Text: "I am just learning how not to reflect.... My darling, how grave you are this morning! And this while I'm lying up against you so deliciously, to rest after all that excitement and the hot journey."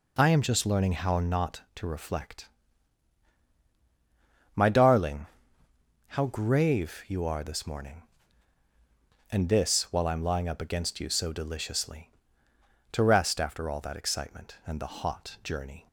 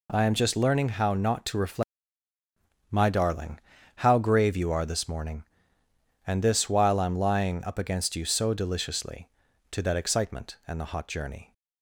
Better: first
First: none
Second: skips "rest after all"; at 9.8 s

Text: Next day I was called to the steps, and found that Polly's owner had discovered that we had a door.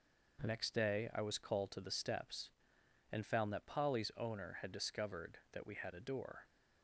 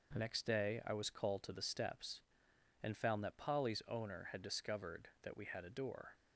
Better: neither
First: none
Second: none

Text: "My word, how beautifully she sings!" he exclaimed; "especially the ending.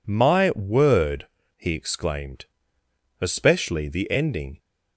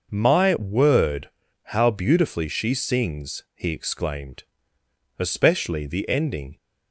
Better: second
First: skips "how beautifully she sings"; at 1.4 s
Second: none

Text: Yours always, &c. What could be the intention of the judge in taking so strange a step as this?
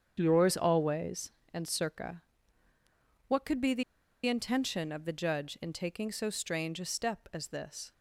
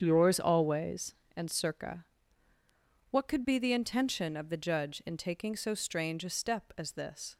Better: second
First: starts louder than the rest; strong; until 1.1 s; 8 dB // pauses between "the" and "intention"; at 3.8 s; 0.43 s long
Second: starts louder than the rest; strong; until 1.0 s; 8 dB

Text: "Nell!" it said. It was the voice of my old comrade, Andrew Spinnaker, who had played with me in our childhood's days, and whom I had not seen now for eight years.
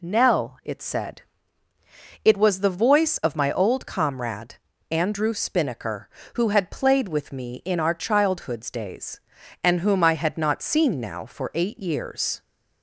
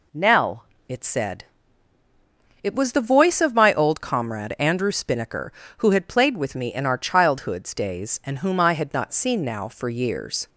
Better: first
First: none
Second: skips "eight"; at 9.8 s

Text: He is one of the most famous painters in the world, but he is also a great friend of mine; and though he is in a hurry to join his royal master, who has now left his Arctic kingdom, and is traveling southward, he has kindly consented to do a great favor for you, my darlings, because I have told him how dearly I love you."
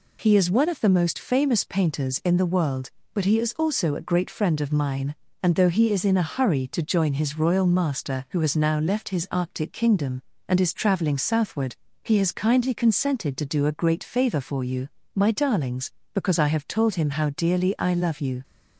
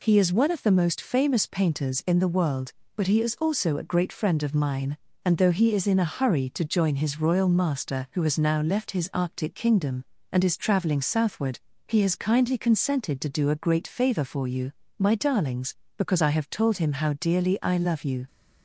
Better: neither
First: none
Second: none

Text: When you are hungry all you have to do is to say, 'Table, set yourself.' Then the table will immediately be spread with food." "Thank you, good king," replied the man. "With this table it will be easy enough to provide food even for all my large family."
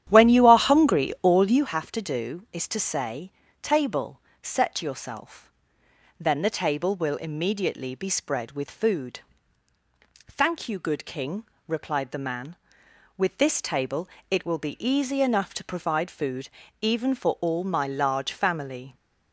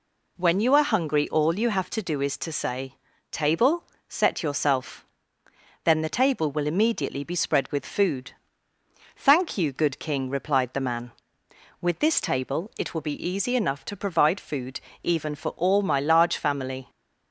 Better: second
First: starts louder than the rest; strong; until 1.8 s; 10.5 dB // pauses between "table" and "it"; slight; at 14.0 s; 0.22 s long // pauses between "food" and "even"; slight; at 16.4 s; 0.32 s long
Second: pauses between "food" and "even"; slight; at 14.8 s; 0.20 s long

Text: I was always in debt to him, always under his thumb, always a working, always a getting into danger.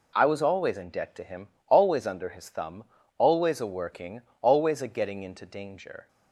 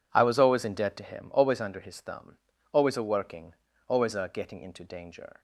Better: neither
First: none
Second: none

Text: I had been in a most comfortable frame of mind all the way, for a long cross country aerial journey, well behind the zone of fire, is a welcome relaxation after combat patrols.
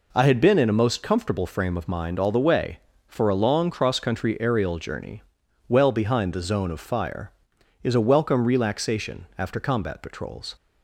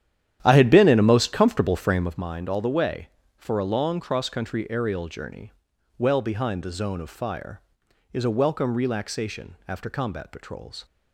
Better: first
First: none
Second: starts louder than the rest; strong; until 2.3 s; 10.5 dB

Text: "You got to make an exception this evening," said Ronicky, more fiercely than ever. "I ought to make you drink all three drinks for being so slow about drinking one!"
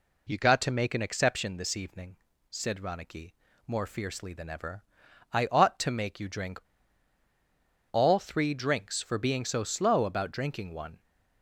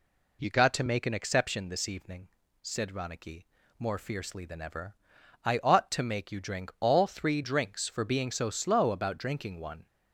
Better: second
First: pauses between "drink" and "all"; strong; at 6.5 s; 1.3 s long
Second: none

